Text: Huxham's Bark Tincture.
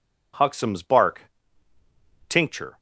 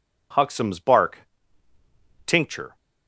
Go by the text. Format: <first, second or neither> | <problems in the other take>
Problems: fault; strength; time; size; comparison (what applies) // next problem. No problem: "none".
neither | pauses between "Bark" and "Tincture"; noticeable; the same in both